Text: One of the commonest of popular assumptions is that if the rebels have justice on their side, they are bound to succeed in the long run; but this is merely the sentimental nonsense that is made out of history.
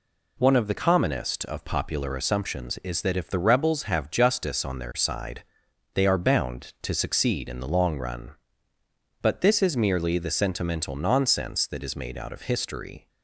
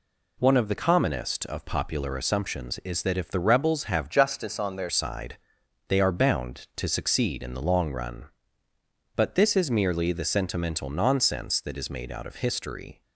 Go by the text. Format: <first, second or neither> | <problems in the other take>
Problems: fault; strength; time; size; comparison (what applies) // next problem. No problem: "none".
first | changes voice from "justice" to "their"; from 4.1 to 4.8 s; 0.7 s long